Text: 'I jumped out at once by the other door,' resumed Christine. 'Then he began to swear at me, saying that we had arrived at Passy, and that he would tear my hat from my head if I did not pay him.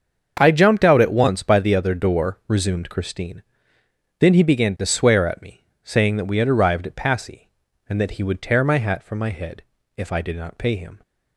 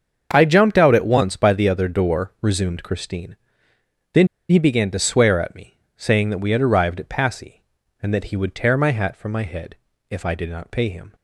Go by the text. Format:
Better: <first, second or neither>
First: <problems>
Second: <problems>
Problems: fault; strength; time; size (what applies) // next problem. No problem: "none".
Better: first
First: starts louder than the rest; until 1.4 s; 7 dB // pauses between "head" and "if"; slight; at 9.6 s; 0.34 s long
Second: starts louder than the rest; until 1.3 s; 7 dB // pauses between "Then" and "he"; slight; at 4.2 s; 0.22 s long // pauses between "head" and "if"; slight; at 9.7 s; 0.34 s long